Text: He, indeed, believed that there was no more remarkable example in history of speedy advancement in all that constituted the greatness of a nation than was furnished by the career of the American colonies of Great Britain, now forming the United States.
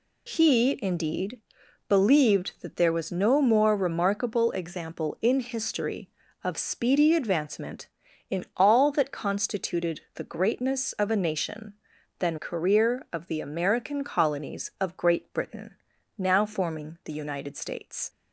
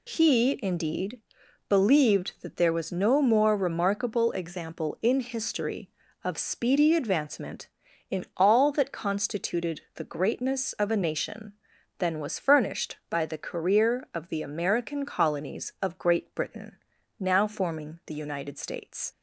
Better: second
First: skips "was furnished by the"; at 12.3 s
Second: none

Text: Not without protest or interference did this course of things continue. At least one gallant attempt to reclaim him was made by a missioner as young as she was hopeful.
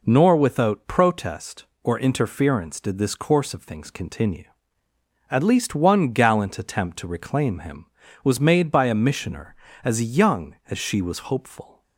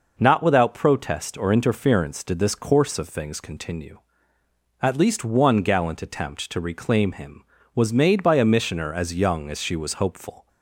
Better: second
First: says "Nor" for "Not"; at 0.0 s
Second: none

